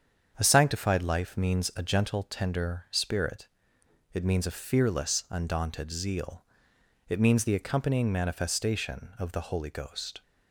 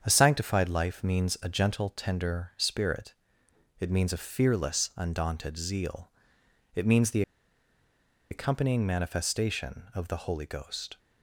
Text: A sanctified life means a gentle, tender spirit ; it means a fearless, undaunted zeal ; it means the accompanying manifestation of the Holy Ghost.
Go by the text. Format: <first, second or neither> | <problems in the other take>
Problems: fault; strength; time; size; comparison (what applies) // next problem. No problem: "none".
first | starts louder than the rest; strong; until 1.0 s; 7.5 dB; strong in the first // pauses between "the" and "accompanying"; at 7.2 s; 1.0 s long